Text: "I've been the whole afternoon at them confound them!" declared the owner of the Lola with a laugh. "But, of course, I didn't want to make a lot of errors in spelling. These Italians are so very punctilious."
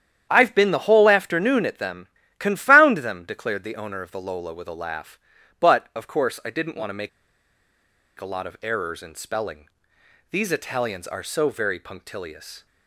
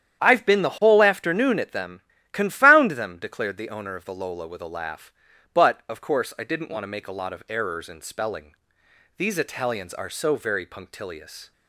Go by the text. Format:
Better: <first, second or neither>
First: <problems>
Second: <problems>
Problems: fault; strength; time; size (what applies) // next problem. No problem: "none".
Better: second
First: starts louder than the rest; strong; until 1.3 s; 9.5 dB // pauses between "them" and "confound"; slight; at 2.0 s; 0.30 s long // pauses between "make" and "a"; at 7.0 s; 1.0 s long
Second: starts louder than the rest; strong; until 1.2 s; 9.5 dB // pauses between "them" and "confound"; slight; at 2.0 s; 0.30 s long